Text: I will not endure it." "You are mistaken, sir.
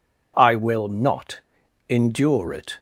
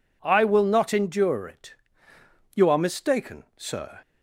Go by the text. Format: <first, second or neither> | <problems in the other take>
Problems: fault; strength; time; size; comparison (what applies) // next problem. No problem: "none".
second | pauses between "not" and "endure"; noticeable; at 1.3 s; 0.50 s long // stops before "You are mistaken sir"; at 2.7 s